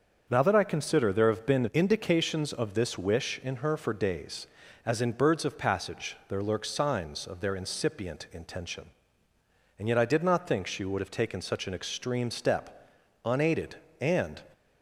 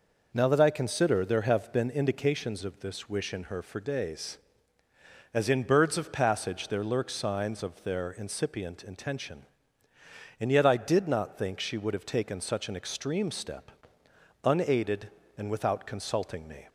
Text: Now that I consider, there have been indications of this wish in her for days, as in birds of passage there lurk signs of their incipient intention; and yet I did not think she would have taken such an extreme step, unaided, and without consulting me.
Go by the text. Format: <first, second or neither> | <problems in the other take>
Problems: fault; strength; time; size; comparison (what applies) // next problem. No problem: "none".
second | starts louder than the rest; until 1.3 s; 7 dB // stops before "without consulting me"; at 14.5 s